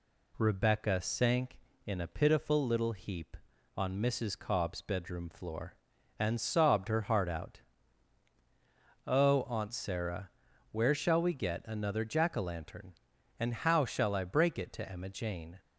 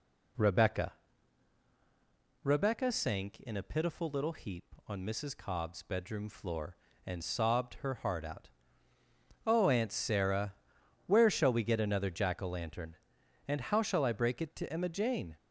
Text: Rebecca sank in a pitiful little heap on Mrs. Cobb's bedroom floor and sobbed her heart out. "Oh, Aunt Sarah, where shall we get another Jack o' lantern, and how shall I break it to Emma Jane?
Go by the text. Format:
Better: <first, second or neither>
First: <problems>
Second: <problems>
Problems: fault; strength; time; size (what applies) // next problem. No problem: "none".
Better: first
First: none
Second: says "Rebecca" twice; at 2.4 s